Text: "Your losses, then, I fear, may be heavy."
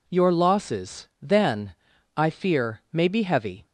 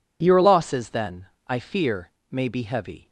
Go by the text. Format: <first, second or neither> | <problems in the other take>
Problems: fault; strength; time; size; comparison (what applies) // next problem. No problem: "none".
neither | none